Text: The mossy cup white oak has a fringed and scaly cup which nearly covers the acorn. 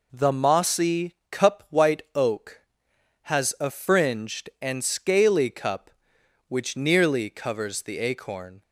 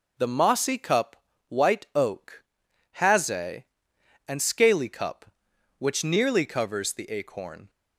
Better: first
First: none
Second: pauses between "cup" and "white"; slight; at 1.1 s; 0.32 s long // skips "fringed"; at 3.9 s

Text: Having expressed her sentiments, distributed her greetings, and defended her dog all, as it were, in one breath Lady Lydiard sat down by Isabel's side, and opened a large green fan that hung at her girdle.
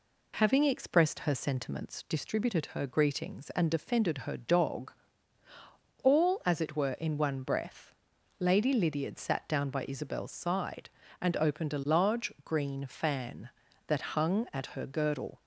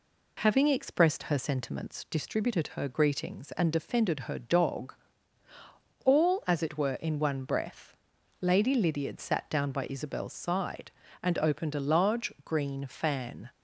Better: first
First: pauses between "dog" and "all"; at 4.9 s; 1.1 s long // pauses between "breath" and "Lady"; noticeable; at 7.9 s; 0.46 s long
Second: pauses between "dog" and "all"; at 4.9 s; 1.1 s long // pauses between "breath" and "Lady"; noticeable; at 7.9 s; 0.46 s long // stops before "that hung at her girdle"; at 13.5 s

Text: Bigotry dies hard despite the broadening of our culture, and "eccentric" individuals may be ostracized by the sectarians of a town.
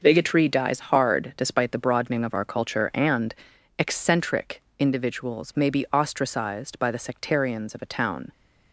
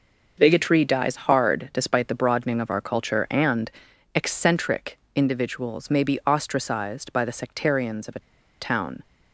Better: first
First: pauses between "and" and "eccentric"; at 3.3 s; 0.42 s long // pauses between "eccentric" and "individuals"; slight; at 4.6 s; 0.20 s long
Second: pauses between "and" and "eccentric"; at 3.7 s; 0.42 s long // pauses between "eccentric" and "individuals"; slight; at 4.9 s; 0.20 s long // pauses between "a" and "town"; at 8.2 s; 0.37 s long

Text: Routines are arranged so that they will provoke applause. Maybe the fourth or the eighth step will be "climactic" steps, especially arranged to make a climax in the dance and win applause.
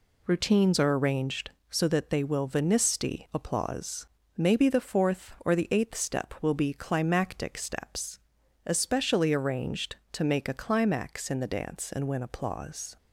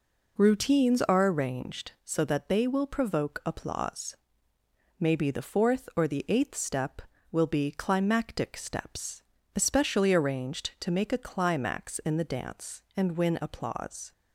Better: second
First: says "venisti" for "provoke"; at 2.4 s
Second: none

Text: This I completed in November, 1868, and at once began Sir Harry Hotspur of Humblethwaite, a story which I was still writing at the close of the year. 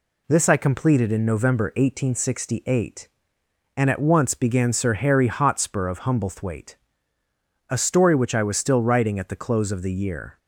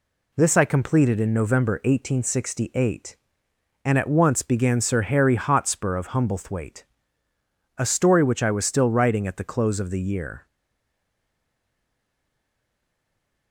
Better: first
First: none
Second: stays silent after the last word; strong; from 10.4 s on; 3.1 s long

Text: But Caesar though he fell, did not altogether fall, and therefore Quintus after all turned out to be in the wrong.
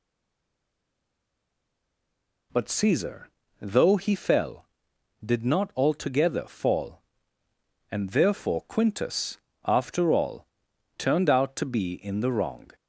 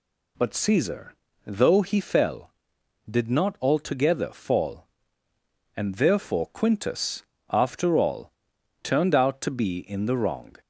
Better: second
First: stays silent before the first word; until 2.5 s; 2.5 s long // pauses between "Caesar" and "though"; slight; at 3.2 s; 0.34 s long // pauses between "Quintus" and "after"; slight; at 9.3 s; 0.30 s long // pauses between "all" and "turned"; noticeable; at 10.4 s; 0.50 s long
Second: pauses between "Caesar" and "though"; slight; at 1.1 s; 0.34 s long // pauses between "Quintus" and "after"; slight; at 7.2 s; 0.30 s long // pauses between "all" and "turned"; noticeable; at 8.3 s; 0.50 s long

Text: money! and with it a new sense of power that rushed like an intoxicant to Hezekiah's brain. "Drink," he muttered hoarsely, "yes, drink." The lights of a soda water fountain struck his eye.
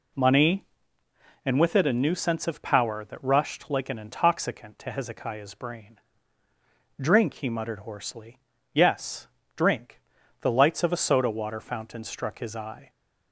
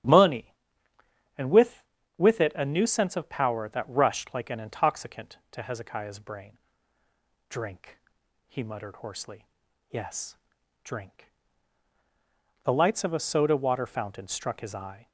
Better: first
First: none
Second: starts louder than the rest; strong; until 2.2 s; 10.5 dB // says "with" twice; at 2.1 s

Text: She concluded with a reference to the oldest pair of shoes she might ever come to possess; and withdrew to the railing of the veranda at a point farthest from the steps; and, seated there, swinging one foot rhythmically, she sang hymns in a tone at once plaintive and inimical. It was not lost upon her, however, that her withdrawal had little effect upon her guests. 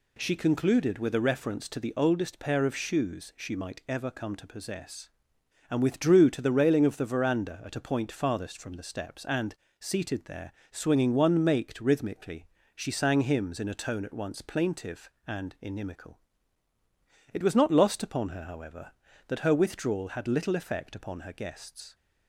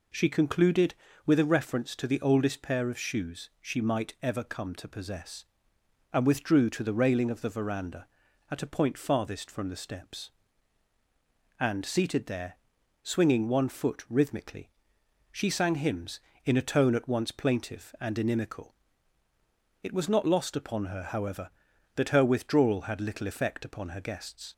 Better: second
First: says "maked" for "foot"; at 11.4 s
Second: none

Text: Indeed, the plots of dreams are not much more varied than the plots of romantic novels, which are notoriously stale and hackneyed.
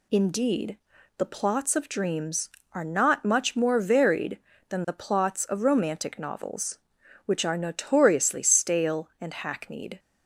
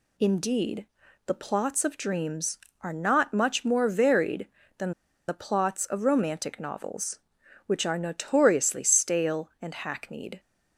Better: first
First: none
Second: pauses between "than" and "the"; at 4.9 s; 0.37 s long

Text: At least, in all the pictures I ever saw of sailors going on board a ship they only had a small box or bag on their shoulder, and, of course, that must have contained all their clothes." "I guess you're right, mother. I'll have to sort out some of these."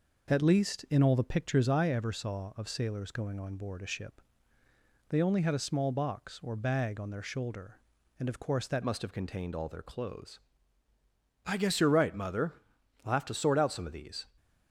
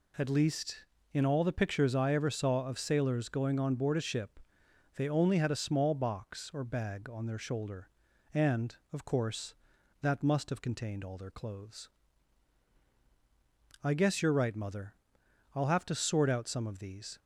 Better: second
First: pauses between "ship" and "they"; noticeable; at 4.2 s; 0.88 s long // changes voice at "must"; from 8.8 s on; 5.4 s long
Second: pauses between "ship" and "they"; noticeable; at 4.3 s; 0.58 s long

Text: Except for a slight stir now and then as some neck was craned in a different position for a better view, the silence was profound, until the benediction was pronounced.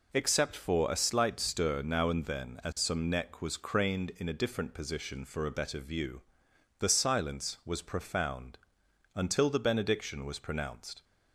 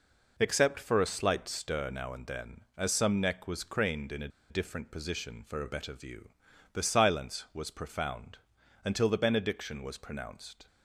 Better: first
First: none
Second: pauses between "a" and "different"; slight; at 4.2 s; 0.21 s long

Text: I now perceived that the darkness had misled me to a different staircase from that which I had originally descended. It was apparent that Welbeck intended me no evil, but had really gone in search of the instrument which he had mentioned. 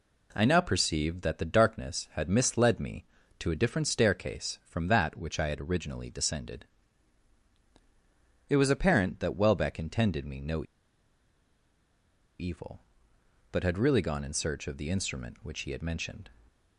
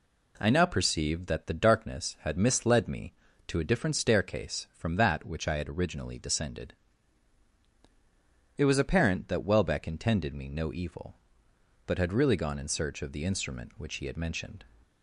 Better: second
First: pauses between "no" and "evil"; strong; at 10.6 s; 1.7 s long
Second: none

